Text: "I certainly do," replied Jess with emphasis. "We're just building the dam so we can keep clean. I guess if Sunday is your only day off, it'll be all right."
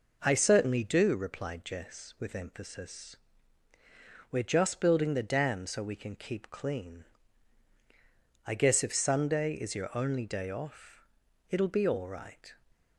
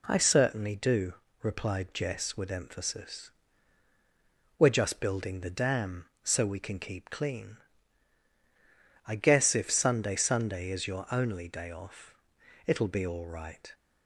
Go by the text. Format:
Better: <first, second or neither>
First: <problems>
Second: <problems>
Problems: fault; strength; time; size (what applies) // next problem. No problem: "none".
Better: first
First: none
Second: says "Sunday" twice; at 10.1 s